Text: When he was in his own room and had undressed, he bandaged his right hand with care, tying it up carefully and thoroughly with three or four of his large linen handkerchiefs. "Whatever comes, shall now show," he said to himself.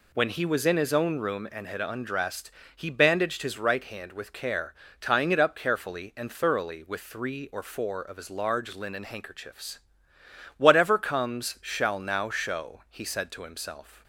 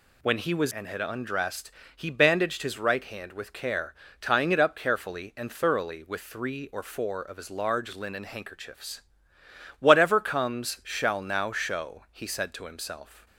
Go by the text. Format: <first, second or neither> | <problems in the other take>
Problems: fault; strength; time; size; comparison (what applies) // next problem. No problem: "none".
first | skips "in his own room"; at 0.7 s